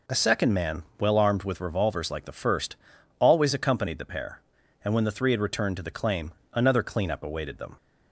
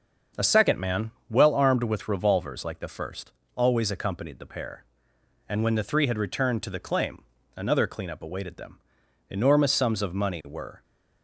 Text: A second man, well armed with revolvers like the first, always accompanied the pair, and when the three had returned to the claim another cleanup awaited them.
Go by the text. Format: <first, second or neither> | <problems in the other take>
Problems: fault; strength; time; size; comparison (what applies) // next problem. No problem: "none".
first | starts louder than the rest; until 1.5 s; 6.5 dB // pauses between "claim" and "another"; slight; at 7.2 s; 0.34 s long; slight in the first // goes on to say "Enormous sums of money were"; from 9.2 s on; 1.5 s long